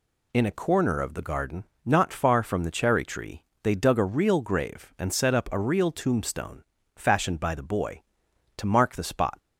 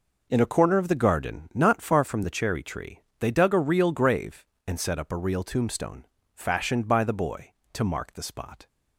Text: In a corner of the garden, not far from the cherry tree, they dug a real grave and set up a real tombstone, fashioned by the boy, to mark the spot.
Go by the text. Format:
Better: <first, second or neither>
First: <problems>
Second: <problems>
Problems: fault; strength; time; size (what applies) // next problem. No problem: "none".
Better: neither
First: none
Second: none